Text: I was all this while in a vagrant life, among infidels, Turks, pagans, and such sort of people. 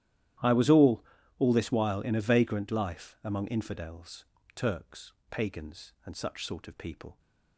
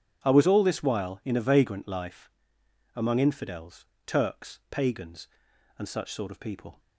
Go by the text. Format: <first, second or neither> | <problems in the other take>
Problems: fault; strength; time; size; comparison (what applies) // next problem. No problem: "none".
second | starts louder than the rest; strong; until 1.7 s; 12.5 dB; strong in the second // says "all" twice; at 1.4 s